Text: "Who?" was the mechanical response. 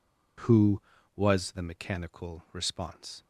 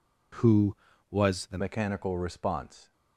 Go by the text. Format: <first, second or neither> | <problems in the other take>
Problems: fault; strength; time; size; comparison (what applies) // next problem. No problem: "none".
first | changes voice at "mechanical"; from 1.5 s on; 1.4 s long